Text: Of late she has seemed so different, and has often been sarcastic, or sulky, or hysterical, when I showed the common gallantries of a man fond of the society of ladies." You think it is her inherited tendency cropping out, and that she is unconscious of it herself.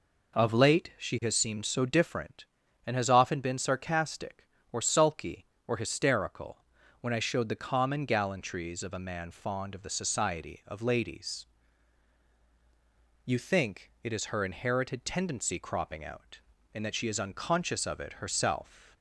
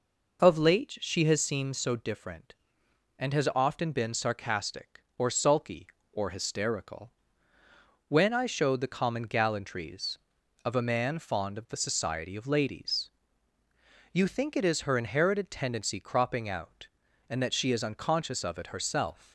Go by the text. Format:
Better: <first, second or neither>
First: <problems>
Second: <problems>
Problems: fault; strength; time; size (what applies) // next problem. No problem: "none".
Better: neither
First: none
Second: none